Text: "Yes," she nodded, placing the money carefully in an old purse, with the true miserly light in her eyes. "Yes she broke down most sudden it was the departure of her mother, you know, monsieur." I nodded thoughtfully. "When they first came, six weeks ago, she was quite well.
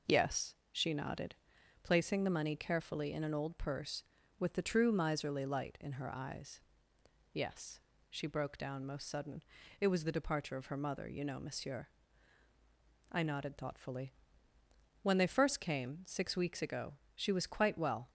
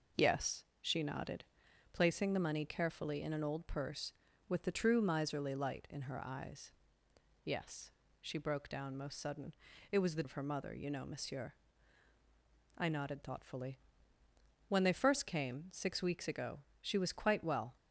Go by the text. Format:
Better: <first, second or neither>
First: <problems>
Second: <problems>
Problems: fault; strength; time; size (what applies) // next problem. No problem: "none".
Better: first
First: pauses between "Yes" and "she"; slight; at 7.8 s; 0.30 s long // pauses between "sudden" and "it"; at 9.4 s; 0.38 s long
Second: pauses between "Yes" and "she"; slight; at 7.9 s; 0.30 s long // pauses between "sudden" and "it"; at 9.5 s; 0.38 s long // skips "departure"; at 10.2 s